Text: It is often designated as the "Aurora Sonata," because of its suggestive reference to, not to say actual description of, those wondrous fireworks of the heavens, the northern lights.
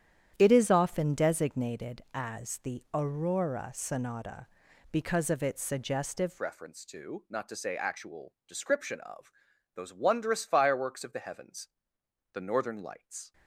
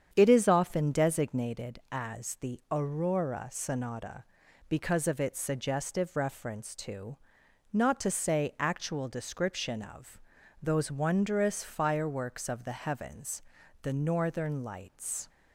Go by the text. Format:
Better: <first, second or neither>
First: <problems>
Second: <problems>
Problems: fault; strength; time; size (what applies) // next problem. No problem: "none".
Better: second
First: starts louder than the rest; strong; until 1.3 s; 9.5 dB // changes voice at "reference"; from 6.4 s on; 6.9 s long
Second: starts louder than the rest; strong; until 1.1 s; 8 dB